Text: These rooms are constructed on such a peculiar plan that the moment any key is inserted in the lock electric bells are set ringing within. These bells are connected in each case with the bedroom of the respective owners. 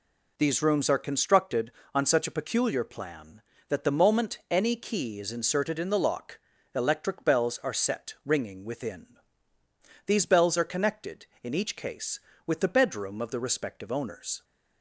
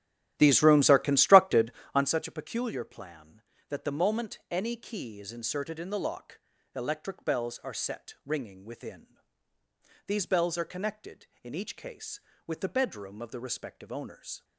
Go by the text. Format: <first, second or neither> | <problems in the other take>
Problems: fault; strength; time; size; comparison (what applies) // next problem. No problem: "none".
first | starts louder than the rest; strong; until 2.1 s; 12.5 dB // pauses between "lock" and "electric"; slight; at 6.3 s; 0.36 s long; slight in the first